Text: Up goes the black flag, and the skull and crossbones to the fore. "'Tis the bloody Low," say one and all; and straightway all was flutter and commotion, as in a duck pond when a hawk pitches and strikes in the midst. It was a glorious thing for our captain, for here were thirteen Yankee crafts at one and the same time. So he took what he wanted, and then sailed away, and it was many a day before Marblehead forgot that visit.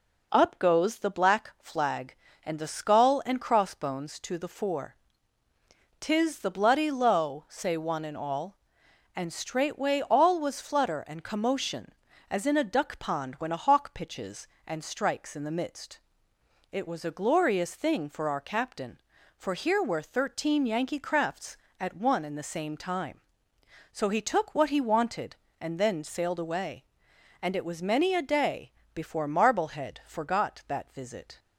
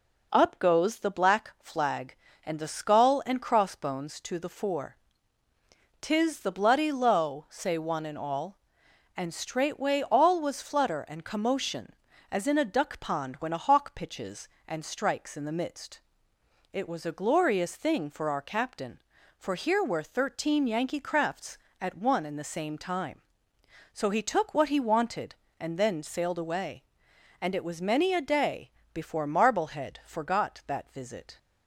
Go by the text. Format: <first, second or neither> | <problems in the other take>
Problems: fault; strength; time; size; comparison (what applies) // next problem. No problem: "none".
neither | pauses between "day" and "before"; slight; the same in both